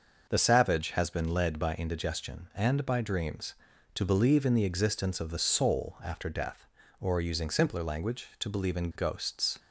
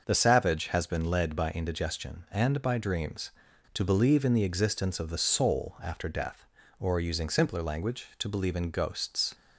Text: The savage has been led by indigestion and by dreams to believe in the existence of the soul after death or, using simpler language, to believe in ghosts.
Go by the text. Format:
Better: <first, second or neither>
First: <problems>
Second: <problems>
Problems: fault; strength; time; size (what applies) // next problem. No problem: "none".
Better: neither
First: starts louder than the rest; until 1.3 s; 6 dB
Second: starts louder than the rest; noticeable; until 1.0 s; 6 dB